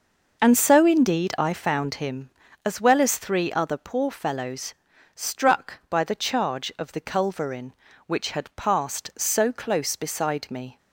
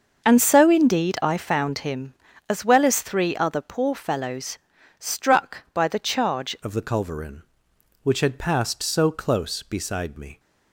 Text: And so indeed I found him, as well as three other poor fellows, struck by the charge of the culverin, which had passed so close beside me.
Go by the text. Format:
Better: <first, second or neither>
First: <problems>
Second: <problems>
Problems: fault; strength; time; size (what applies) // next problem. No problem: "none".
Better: first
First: none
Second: starts louder than the rest; until 1.2 s; 6.5 dB // changes voice at "of"; from 6.6 s on; 3.7 s long